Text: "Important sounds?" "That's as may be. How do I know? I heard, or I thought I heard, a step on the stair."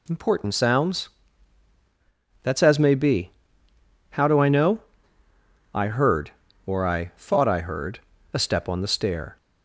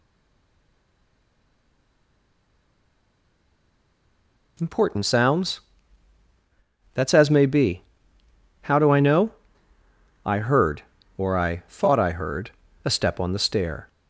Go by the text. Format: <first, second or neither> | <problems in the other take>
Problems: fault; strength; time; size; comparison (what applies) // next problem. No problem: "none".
first | stays silent before the first word; strong; until 4.5 s; 4.5 s long